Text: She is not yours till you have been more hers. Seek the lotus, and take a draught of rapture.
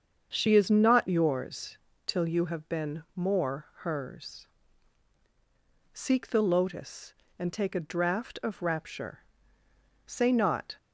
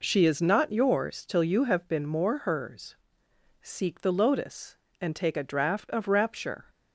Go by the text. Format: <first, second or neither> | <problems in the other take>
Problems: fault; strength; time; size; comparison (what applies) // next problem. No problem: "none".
second | starts louder than the rest; until 1.3 s; 7 dB // pauses between "yours" and "till"; slight; at 1.7 s; 0.30 s long // goes on to say "Say not"; noticeable; from 10.0 s on; 0.72 s long